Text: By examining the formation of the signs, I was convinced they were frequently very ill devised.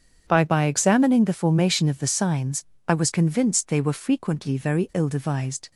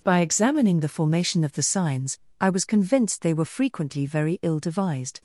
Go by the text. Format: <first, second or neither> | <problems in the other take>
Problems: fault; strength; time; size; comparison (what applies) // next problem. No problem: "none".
second | starts louder than the rest; strong; until 1.2 s; 7.5 dB // says "By" twice; at 0.4 s